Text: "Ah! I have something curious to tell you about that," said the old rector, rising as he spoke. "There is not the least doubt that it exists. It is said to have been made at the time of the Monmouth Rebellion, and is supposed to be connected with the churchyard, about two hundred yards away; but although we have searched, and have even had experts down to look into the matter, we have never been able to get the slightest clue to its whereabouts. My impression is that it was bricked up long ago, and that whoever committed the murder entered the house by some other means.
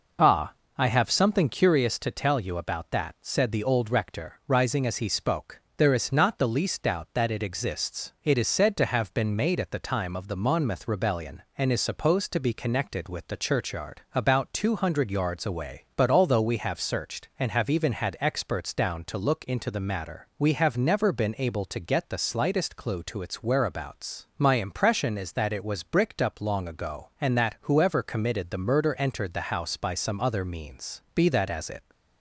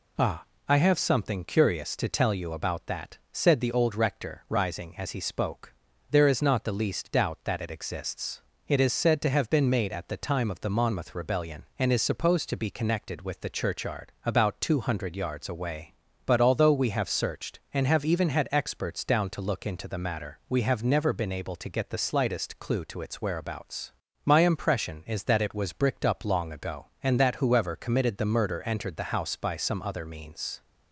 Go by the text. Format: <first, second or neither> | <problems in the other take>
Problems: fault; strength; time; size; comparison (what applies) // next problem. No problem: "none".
second | goes on to say "Be that as it"; noticeable; from 31.1 s on; 0.76 s long